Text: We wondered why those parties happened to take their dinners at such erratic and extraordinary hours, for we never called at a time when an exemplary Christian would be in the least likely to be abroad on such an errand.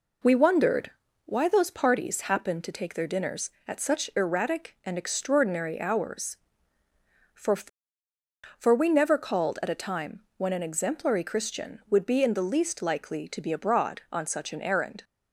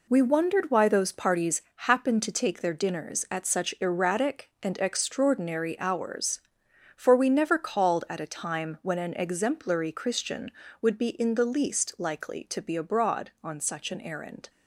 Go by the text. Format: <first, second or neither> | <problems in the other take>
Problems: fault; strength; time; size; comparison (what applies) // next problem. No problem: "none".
second | pauses between "wondered" and "why"; slight; at 0.9 s; 0.34 s long // says "for" twice; at 8.5 s // pauses between "time" and "when"; slight; at 10.2 s; 0.16 s long